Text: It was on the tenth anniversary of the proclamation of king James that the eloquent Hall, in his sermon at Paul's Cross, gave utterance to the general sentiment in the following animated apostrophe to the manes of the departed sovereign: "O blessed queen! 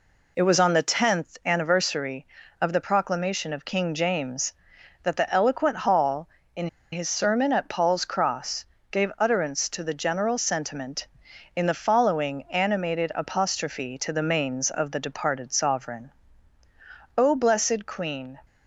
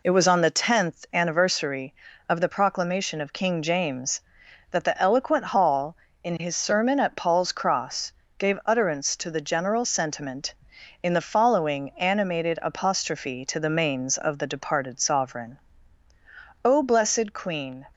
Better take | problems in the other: second | pauses between "in" and "his"; slight; at 6.6 s; 0.25 s long

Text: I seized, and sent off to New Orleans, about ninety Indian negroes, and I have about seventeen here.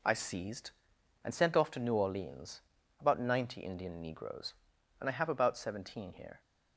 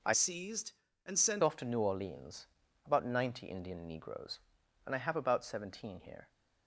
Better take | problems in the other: first | changes voice from "seized" to "sent"; from 0.1 to 1.4 s; 1.3 s long

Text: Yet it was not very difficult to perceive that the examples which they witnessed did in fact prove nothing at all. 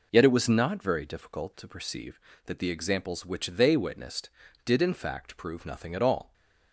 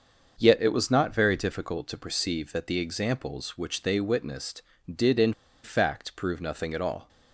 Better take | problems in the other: first | starts louder than the rest; until 1.3 s; 6.5 dB // pauses between "in" and "fact"; slight; at 5.3 s; 0.30 s long

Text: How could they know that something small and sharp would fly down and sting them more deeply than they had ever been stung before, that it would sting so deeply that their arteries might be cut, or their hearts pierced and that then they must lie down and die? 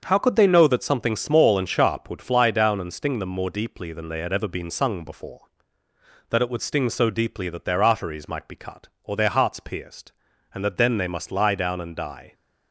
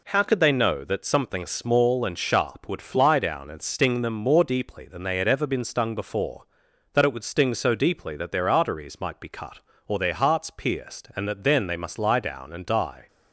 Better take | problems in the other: second | starts louder than the rest; until 1.0 s; 7 dB // says "sung" for "stung"; at 4.6 s

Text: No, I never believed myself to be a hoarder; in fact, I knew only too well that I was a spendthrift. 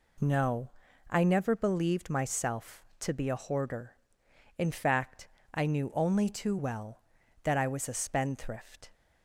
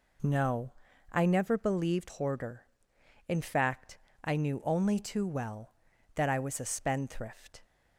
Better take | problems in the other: first | skips "myself to be a"; at 2.0 s

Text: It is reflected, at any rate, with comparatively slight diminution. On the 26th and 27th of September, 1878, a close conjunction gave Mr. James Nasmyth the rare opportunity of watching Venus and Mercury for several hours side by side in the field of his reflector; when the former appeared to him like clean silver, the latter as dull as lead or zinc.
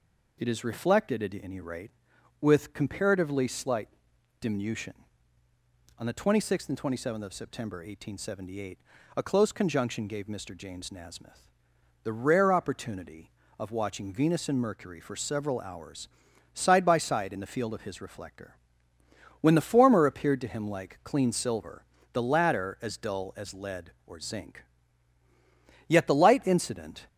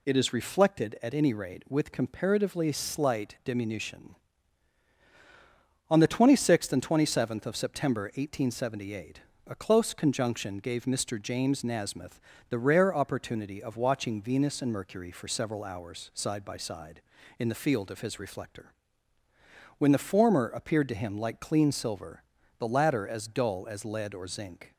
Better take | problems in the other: second | pauses between "slight" and "diminution"; noticeable; at 3.8 s; 0.50 s long // pauses between "Nasmyth" and "the"; noticeable; at 11.4 s; 0.56 s long; slight in the second // pauses between "hours" and "side"; noticeable; at 16.0 s; 0.46 s long // goes on to say "Yet the light incident"; noticeable; from 25.8 s on; 1.1 s long

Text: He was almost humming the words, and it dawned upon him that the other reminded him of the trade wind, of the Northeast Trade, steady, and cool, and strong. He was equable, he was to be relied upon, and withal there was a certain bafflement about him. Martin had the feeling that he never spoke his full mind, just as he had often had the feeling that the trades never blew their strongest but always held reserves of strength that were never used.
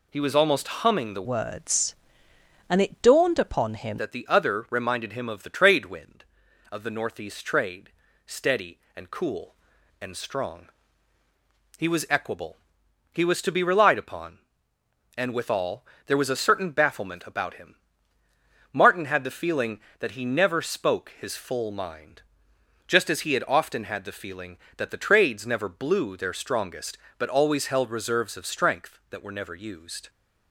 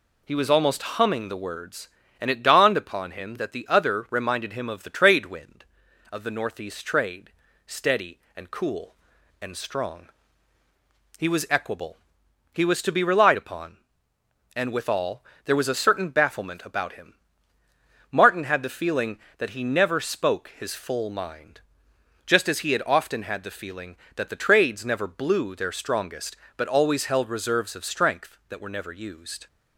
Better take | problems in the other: second | changes voice from "words" to "him"; from 1.2 to 3.9 s; 2.7 s long // pauses between "withal" and "there"; slight; at 15.8 s; 0.22 s long; slight in the second

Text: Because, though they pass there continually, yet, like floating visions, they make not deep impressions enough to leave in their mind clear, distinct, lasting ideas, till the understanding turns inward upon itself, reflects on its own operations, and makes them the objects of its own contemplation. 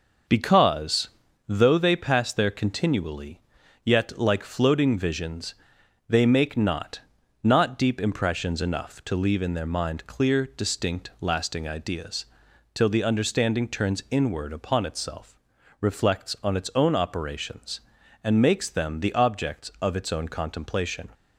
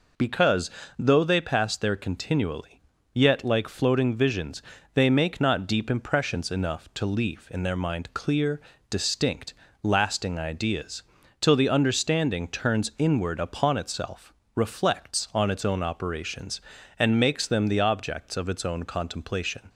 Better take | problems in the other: second | says "not" twice; at 7.4 s

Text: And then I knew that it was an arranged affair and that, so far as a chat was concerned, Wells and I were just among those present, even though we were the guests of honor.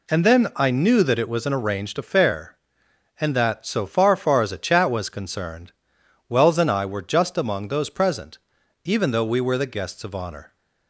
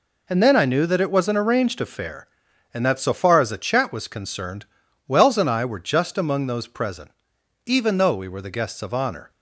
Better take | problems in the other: second | says "far" twice; at 4.1 s

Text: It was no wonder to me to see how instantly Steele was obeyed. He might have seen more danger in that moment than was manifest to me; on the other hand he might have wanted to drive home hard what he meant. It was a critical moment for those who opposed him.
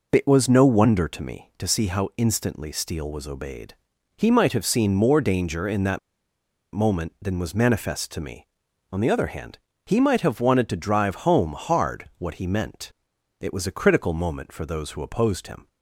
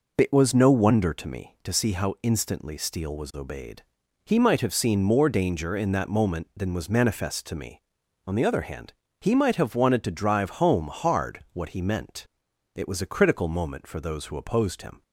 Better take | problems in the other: second | pauses between "that" and "moment"; noticeable; at 5.9 s; 0.74 s long // pauses between "hand" and "he"; slight; at 9.5 s; 0.26 s long; slight in the second

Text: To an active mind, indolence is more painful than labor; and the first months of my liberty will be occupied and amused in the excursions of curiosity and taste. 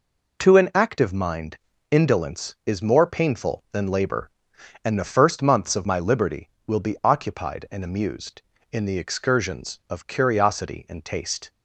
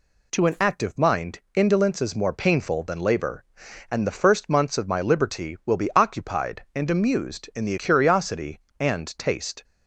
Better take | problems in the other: first | skips "excursions of"; at 7.7 s

